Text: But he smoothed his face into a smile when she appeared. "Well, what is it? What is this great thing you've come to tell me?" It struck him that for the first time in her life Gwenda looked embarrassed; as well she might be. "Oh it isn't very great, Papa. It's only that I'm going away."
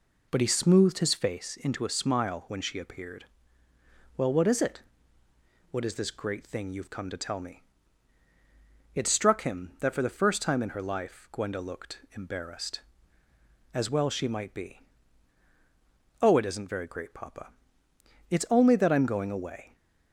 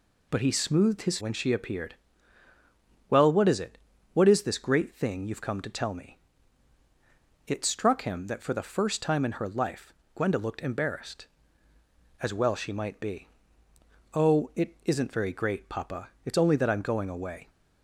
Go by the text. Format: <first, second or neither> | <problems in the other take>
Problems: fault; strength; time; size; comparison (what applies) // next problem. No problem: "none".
first | skips "face into a smile"; at 1.1 s // pauses between "life" and "Gwenda"; slight; at 9.9 s; 0.22 s long